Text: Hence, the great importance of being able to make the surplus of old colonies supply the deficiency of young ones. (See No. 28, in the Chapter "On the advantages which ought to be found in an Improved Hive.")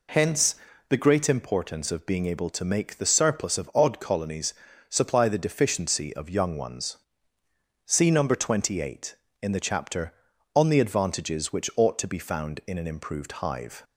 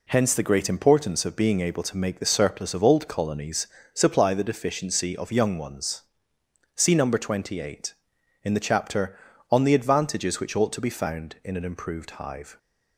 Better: second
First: says "odd" for "old"; at 3.7 s // pauses between "colonies" and "supply"; slight; at 4.5 s; 0.36 s long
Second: pauses between "colonies" and "supply"; slight; at 3.6 s; 0.24 s long

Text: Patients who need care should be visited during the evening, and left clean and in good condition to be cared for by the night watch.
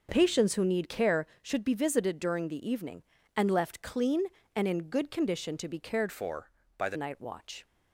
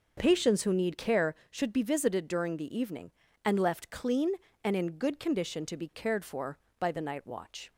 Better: second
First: changes voice from "for" to "the"; from 6.0 to 6.9 s; 0.9 s long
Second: none

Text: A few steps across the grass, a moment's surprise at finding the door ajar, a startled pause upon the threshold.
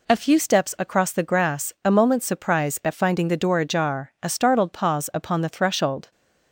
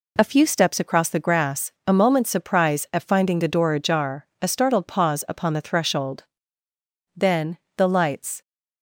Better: first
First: none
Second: goes on to say "Then the lights"; noticeable; from 7.1 s on; 1.2 s long

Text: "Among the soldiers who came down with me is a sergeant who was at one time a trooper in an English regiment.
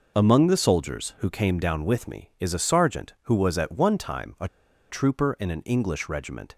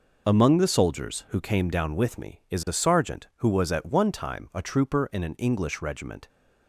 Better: second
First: pauses between "a" and "trooper"; at 4.4 s; 0.43 s long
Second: none

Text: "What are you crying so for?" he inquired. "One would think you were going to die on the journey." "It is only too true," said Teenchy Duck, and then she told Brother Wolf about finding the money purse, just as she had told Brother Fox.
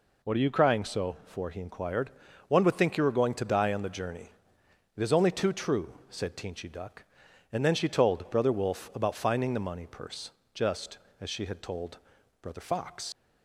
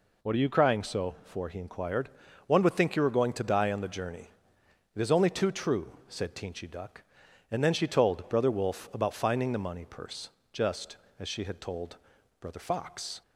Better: second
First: pauses between "told" and "Brother"; at 11.9 s; 0.44 s long // leaves "Fox" unfinished; at 13.1 s; 110 ms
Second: pauses between "told" and "Brother"; at 11.9 s; 0.44 s long

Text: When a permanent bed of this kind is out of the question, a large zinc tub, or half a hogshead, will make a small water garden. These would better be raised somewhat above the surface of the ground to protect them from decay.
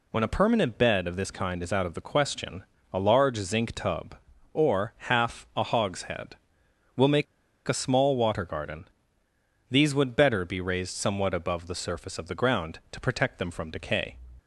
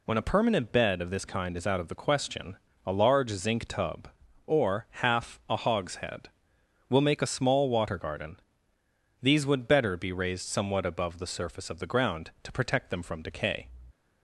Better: second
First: pauses between "make" and "a"; at 7.2 s; 0.43 s long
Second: none

